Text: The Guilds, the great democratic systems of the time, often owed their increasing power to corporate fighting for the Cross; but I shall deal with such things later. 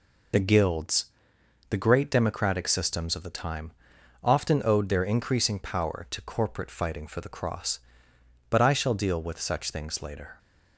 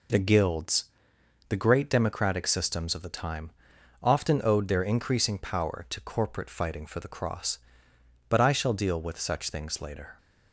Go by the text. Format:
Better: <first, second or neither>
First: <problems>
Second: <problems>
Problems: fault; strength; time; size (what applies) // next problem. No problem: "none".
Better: second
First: loses the start of "The"; at 0.3 s; 30 ms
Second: none